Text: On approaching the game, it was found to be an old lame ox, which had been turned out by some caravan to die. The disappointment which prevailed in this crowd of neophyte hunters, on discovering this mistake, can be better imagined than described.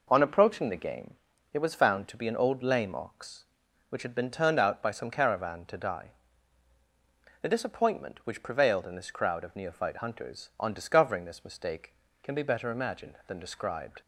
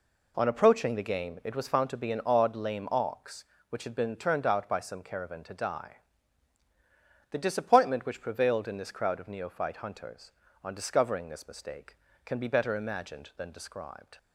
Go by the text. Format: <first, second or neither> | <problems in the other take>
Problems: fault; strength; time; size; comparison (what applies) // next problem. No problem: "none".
first | says "odd" for "old"; at 2.2 s